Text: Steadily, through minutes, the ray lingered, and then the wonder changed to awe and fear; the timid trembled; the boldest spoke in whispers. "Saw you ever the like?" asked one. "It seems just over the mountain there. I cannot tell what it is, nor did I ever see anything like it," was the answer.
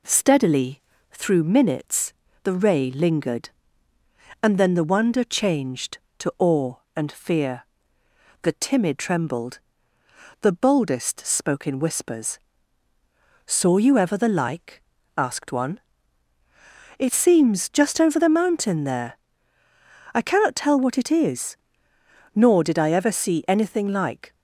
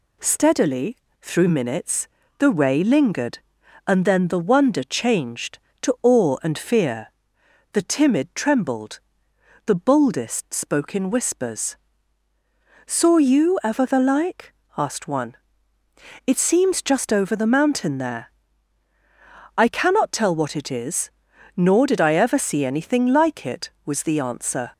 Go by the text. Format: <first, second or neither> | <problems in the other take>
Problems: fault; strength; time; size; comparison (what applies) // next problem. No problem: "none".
second | stops before "it was the answer"; at 24.3 s